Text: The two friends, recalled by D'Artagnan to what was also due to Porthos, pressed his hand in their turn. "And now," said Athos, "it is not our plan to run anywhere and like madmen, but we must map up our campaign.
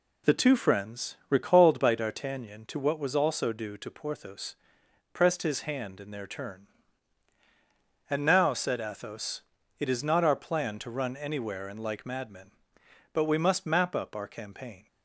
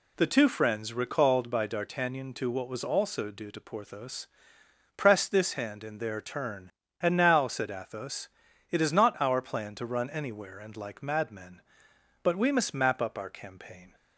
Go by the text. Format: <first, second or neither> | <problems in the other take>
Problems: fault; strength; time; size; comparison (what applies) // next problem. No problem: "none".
first | says "this" for "his"; at 5.3 s